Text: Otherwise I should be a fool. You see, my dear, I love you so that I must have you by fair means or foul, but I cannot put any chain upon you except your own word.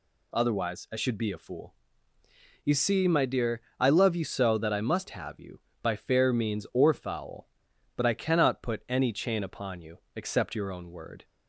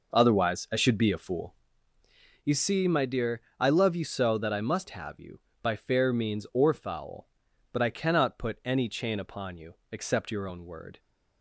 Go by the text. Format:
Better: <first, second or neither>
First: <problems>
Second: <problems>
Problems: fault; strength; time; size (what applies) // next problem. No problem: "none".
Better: first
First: pauses between "you" and "except"; slight; at 9.9 s; 0.18 s long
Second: starts louder than the rest; noticeable; until 1.8 s; 5 dB // pauses between "you" and "except"; slight; at 9.7 s; 0.18 s long